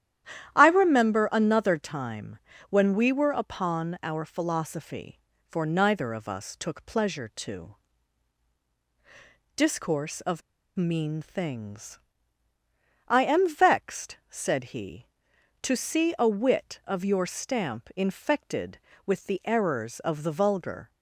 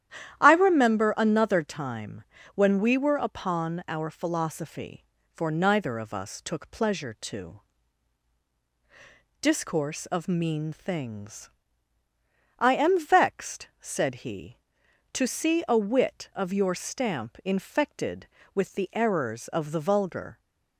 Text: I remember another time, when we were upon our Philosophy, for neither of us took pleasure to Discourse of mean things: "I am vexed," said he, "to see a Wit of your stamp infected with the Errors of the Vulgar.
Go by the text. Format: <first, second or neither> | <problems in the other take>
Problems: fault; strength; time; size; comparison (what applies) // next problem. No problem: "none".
second | starts louder than the rest; strong; until 1.5 s; 11 dB; strong in the second // pauses between "to" and "Discourse"; strong; at 7.7 s; 1.8 s long; strong in the second // pauses between "of" and "mean"; slight; at 10.4 s; 0.35 s long